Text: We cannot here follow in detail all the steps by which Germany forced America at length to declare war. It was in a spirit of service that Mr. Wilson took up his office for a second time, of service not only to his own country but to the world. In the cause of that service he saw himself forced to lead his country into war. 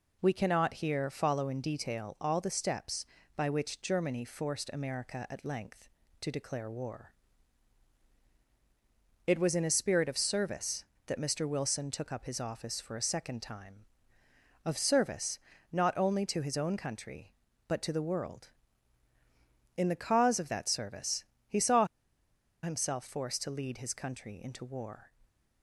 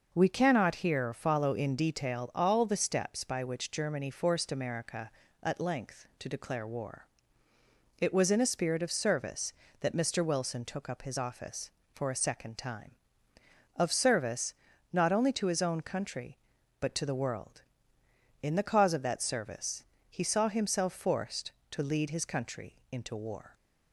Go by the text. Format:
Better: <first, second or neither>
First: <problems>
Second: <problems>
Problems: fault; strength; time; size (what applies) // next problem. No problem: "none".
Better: second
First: pauses between "service" and "not"; slight; at 15.3 s; 0.32 s long // pauses between "service" and "he"; slight; at 21.2 s; 0.24 s long // pauses between "saw" and "himself"; noticeable; at 21.8 s; 0.78 s long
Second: pauses between "service" and "not"; slight; at 14.5 s; 0.36 s long // pauses between "service" and "he"; slight; at 19.8 s; 0.26 s long